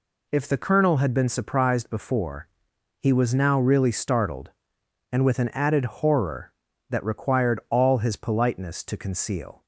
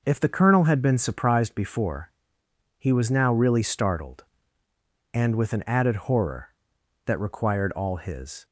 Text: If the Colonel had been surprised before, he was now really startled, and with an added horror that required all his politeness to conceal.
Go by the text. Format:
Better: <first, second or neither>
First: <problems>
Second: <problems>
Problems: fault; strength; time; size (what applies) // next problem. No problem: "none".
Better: first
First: none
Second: stops before "politeness to conceal"; at 8.4 s